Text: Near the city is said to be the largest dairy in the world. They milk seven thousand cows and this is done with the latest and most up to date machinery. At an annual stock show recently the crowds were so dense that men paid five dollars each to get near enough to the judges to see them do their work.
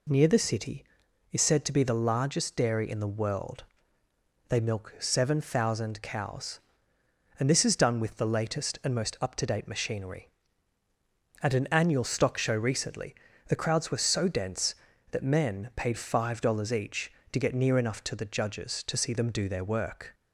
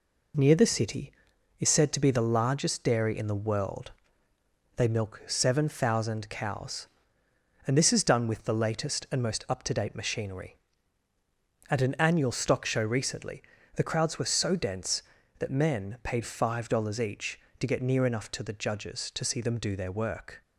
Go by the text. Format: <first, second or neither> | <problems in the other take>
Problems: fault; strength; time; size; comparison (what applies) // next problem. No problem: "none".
first | gets quieter; noticeable; throughout; 4.5 dB // pauses between "recently" and "the"; slight; at 13.4 s; 0.34 s long; slight in the first